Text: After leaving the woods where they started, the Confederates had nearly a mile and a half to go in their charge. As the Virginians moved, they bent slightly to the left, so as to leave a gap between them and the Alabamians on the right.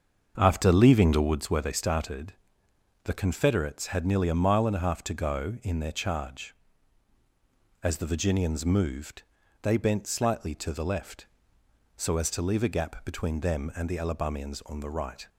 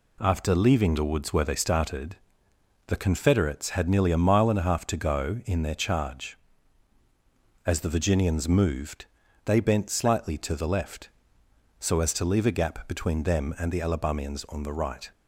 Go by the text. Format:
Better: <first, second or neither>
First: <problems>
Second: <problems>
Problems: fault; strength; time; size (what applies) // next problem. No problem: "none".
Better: second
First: starts louder than the rest; until 1.5 s; 6.5 dB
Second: none